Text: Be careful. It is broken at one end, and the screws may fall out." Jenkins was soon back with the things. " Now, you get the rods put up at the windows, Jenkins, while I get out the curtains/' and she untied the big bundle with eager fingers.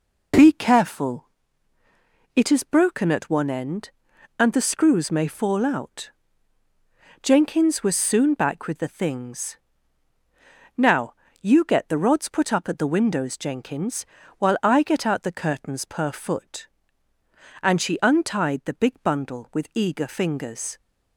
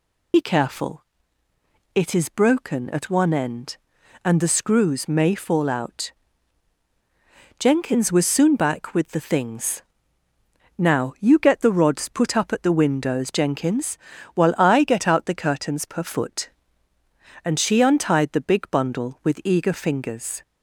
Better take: first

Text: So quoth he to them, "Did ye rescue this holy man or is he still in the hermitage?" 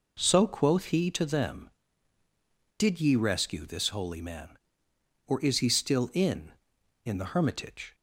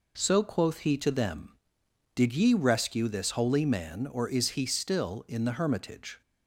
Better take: second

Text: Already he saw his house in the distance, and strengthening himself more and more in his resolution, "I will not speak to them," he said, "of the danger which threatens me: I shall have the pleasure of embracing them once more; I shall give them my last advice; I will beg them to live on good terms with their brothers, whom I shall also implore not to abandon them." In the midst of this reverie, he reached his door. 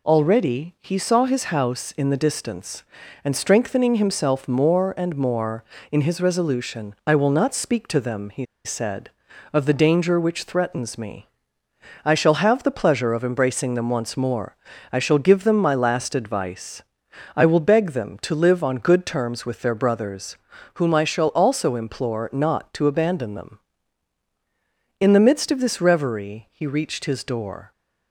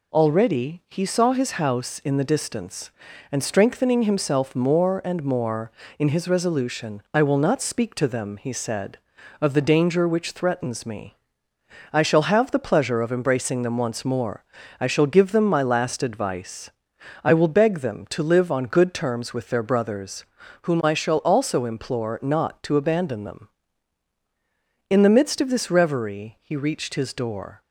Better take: second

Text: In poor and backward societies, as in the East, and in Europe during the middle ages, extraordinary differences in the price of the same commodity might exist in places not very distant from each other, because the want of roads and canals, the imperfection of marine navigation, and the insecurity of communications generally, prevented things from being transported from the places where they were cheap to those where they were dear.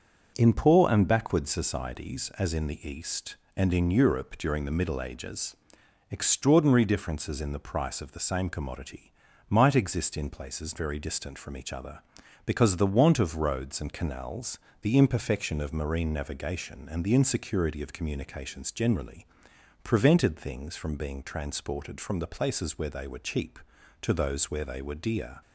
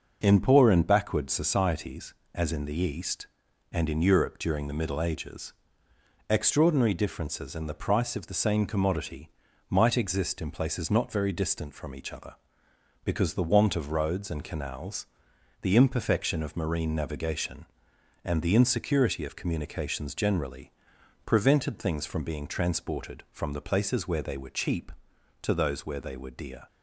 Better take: second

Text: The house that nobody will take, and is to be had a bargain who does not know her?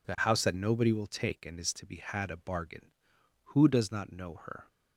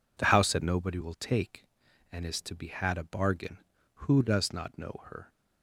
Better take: neither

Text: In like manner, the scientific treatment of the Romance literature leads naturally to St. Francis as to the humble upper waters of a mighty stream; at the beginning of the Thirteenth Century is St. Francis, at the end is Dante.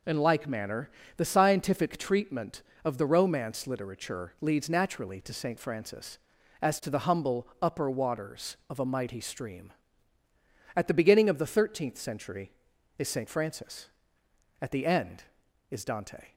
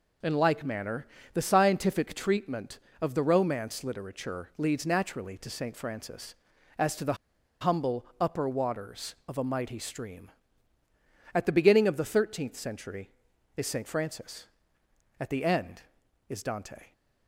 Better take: first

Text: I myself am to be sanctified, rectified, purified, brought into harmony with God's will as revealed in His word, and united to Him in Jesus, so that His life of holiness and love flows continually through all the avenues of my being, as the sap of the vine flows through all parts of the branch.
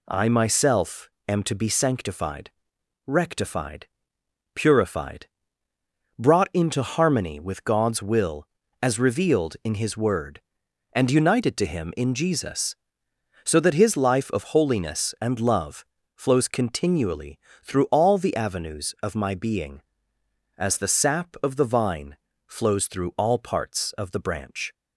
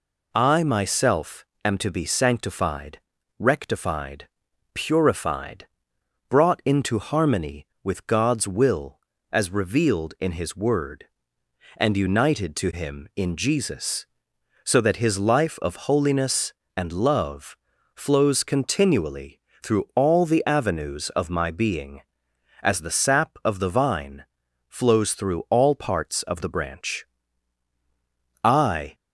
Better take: first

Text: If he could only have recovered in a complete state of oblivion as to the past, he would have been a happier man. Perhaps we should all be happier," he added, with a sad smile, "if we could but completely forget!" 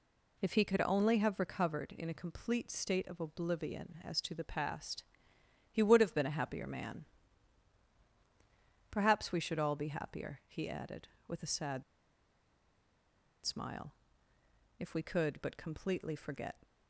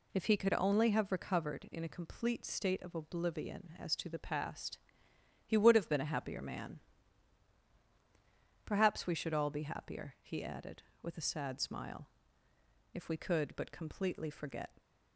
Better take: second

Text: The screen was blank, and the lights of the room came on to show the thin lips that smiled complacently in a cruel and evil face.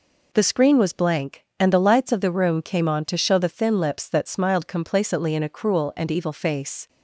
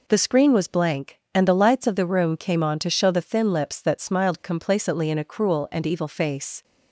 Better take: neither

